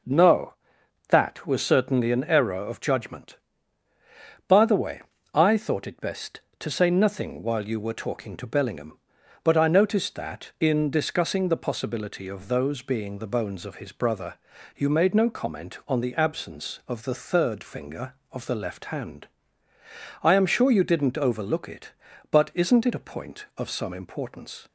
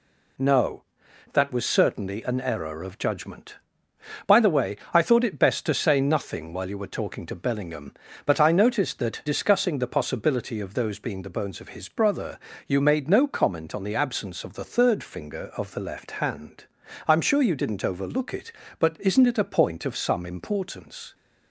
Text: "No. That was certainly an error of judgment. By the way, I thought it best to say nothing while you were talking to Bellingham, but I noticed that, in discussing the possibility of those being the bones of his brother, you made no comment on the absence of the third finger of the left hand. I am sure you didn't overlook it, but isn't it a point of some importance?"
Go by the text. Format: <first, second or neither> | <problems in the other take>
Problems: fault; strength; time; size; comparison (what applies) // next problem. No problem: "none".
first | skips "in"; at 9.2 s